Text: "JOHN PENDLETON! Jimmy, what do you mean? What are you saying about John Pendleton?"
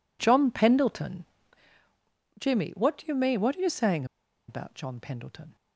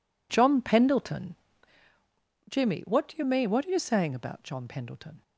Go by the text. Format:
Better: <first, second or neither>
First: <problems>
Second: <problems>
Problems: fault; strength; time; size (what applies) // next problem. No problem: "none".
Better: second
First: pauses between "saying" and "about"; at 4.0 s; 0.44 s long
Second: none